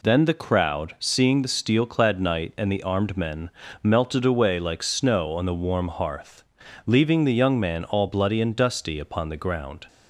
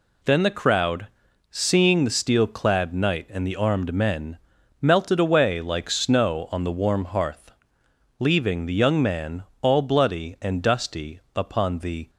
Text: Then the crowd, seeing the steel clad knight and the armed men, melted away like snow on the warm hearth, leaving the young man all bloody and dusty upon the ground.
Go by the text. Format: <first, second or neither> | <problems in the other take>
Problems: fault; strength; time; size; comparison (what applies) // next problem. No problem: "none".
first | pauses between "man" and "all"; slight; at 9.4 s; 0.18 s long // pauses between "dusty" and "upon"; slight; at 11.1 s; 0.16 s long // stops before "ground"; at 12.0 s